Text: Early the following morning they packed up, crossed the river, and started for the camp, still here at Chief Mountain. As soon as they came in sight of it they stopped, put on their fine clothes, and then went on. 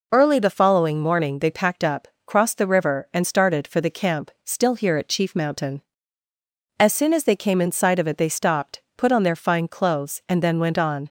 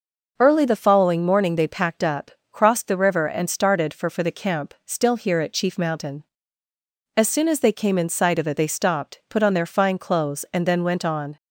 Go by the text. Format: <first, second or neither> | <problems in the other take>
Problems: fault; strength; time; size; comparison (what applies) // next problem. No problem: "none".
first | says "for" twice; at 4.0 s